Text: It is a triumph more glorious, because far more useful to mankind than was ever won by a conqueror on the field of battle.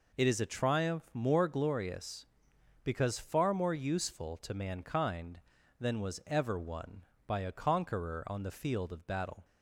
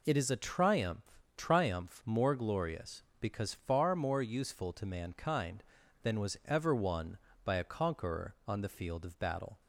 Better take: first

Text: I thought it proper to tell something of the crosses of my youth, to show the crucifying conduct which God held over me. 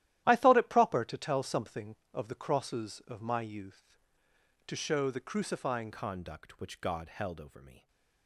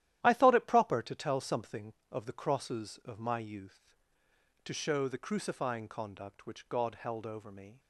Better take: second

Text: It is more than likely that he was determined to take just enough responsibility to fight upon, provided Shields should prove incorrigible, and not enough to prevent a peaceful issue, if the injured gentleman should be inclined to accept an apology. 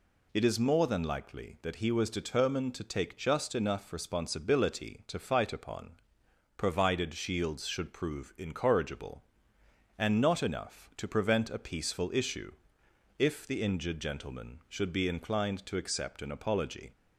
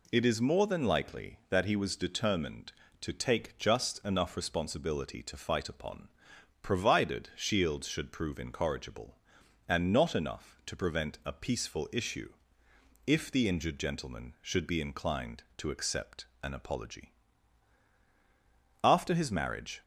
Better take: first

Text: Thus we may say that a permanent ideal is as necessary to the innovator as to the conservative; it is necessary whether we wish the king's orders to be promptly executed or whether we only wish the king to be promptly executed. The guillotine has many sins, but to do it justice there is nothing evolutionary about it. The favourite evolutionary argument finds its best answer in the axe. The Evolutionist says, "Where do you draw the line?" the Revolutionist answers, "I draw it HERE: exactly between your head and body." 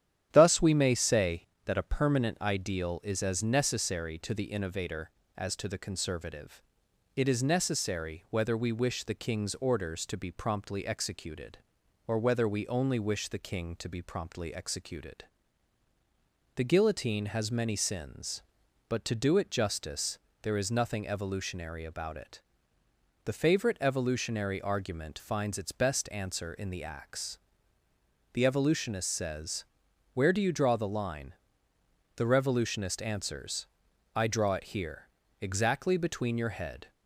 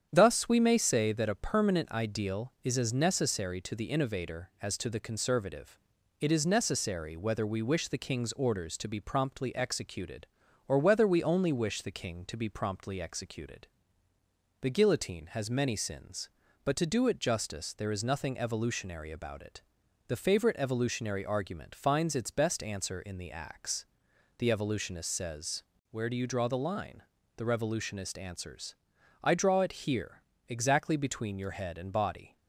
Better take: second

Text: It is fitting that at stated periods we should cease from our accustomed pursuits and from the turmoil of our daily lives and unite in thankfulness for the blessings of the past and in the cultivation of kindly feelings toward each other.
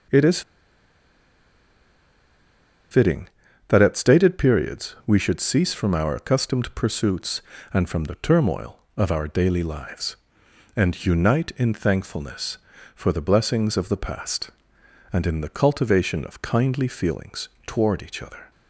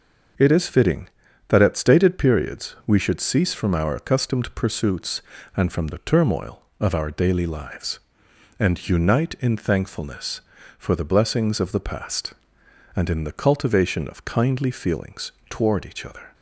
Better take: second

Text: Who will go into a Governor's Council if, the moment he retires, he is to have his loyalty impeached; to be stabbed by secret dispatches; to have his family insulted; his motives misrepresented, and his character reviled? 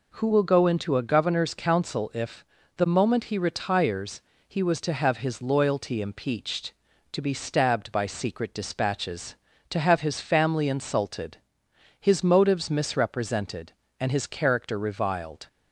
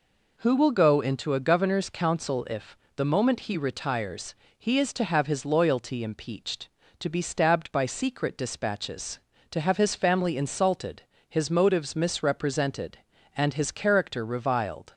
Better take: second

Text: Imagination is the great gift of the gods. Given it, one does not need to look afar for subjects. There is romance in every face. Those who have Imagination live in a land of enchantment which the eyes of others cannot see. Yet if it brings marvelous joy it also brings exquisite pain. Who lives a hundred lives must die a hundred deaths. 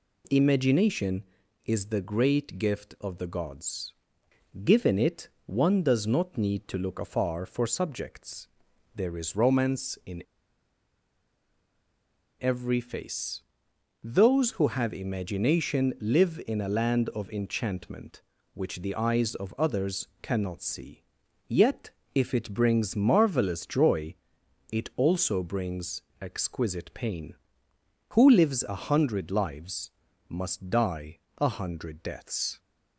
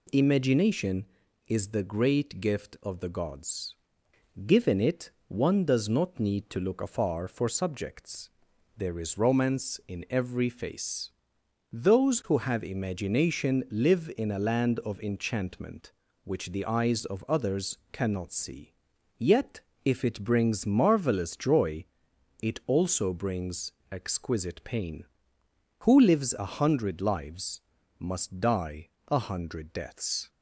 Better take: second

